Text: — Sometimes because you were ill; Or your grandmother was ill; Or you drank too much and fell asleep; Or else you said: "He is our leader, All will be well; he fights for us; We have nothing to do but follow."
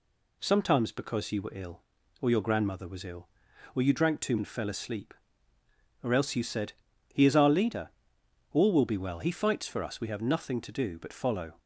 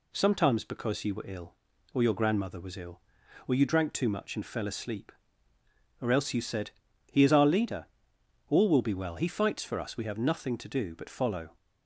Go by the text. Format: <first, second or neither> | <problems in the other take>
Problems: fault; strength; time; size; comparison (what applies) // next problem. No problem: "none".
second | skips "much"; at 4.3 s